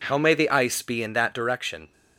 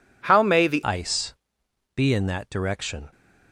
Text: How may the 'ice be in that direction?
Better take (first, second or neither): first